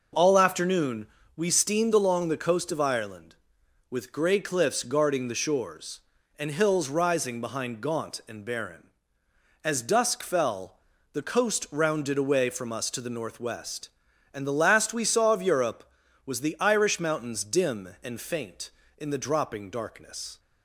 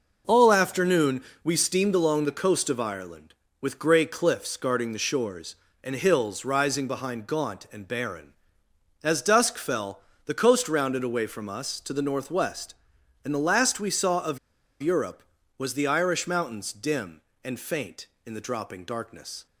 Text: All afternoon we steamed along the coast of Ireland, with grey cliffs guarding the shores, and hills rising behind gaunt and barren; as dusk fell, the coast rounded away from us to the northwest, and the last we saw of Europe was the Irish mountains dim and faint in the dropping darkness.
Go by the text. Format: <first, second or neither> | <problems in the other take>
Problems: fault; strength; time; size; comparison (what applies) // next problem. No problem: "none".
first | pauses between "afternoon" and "we"; slight; at 1.2 s; 0.22 s long; slight in the first // pauses between "of" and "Europe"; at 14.3 s; 0.43 s long